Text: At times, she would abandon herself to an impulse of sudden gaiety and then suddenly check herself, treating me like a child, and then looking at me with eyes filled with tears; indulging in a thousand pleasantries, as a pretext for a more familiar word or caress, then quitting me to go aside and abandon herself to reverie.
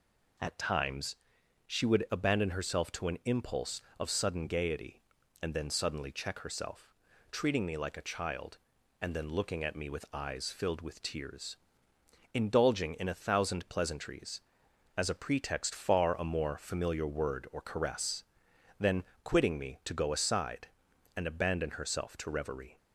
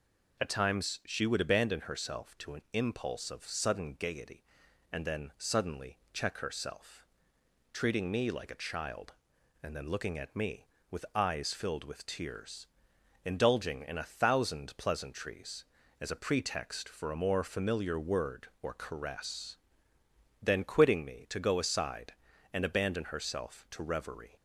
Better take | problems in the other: second | says "far" for "for"; at 15.7 s // pauses between "then" and "quitting"; slight; at 19.0 s; 0.20 s long

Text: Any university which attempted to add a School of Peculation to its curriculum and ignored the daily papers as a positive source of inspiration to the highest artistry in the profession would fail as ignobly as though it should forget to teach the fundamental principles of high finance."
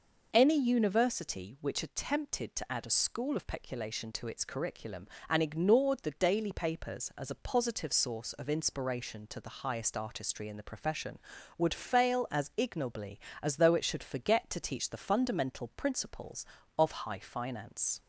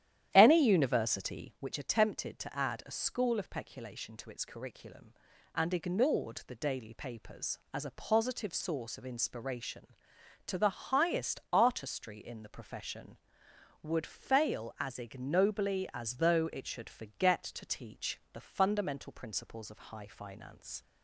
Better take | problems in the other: first | starts louder than the rest; strong; until 1.7 s; 11 dB

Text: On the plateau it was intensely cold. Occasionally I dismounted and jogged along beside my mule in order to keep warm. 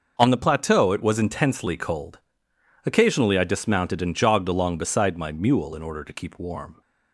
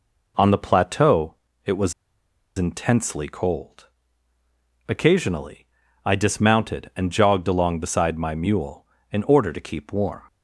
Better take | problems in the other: first | pauses between "plateau" and "it"; slight; at 1.3 s; 0.30 s long // pauses between "was" and "intensely"; noticeable; at 1.9 s; 0.64 s long // pauses between "Occasionally" and "I"; at 5.6 s; 0.38 s long

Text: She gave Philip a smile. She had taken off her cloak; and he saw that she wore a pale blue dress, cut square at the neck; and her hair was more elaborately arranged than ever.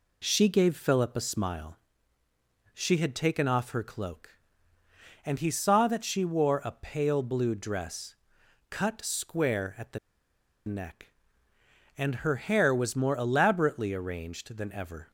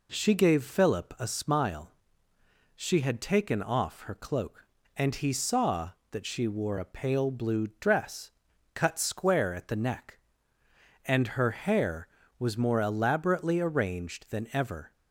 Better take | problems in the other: second | pauses between "the" and "neck"; noticeable; at 9.9 s; 0.67 s long

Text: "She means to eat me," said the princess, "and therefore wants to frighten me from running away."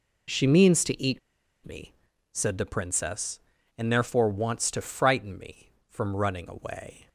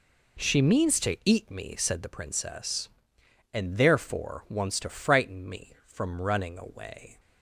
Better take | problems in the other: second | pauses between "eat" and "me"; noticeable; at 1.1 s; 0.46 s long

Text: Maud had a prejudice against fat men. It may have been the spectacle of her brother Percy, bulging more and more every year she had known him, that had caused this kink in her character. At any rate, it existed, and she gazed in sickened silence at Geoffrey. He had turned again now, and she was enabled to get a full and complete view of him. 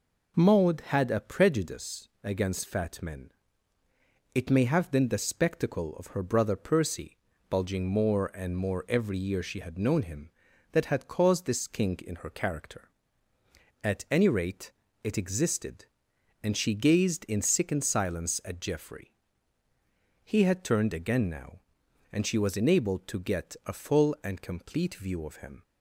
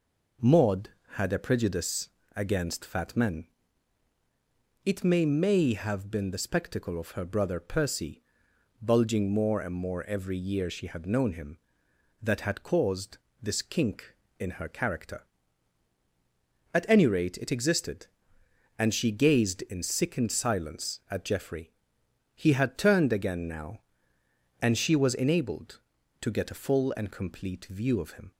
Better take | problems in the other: first | pauses between "prejudice" and "against"; slight; at 2.0 s; 0.26 s long; slight in the first // says "may" twice; at 5.2 s // pauses between "caused" and "this"; slight; at 13.1 s; 0.26 s long

